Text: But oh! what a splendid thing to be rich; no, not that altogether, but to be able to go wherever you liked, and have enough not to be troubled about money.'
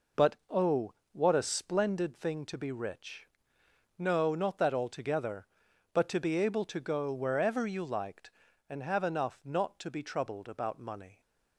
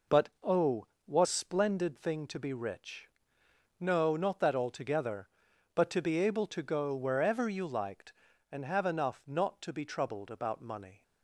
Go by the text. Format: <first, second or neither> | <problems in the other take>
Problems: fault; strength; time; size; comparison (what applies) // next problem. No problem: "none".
first | skips "a"; at 1.2 s